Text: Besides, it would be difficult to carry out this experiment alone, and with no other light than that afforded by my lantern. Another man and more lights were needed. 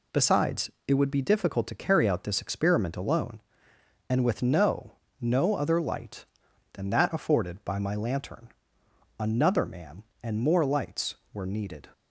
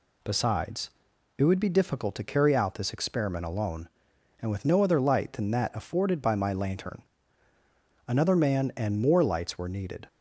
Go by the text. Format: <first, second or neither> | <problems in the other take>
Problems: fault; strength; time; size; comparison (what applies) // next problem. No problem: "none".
second | says "no" twice; at 5.2 s